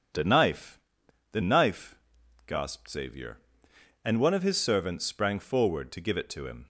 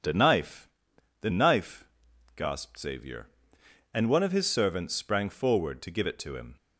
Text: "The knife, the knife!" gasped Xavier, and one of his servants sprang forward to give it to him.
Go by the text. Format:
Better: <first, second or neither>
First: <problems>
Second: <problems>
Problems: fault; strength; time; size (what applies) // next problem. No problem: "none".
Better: neither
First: none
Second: none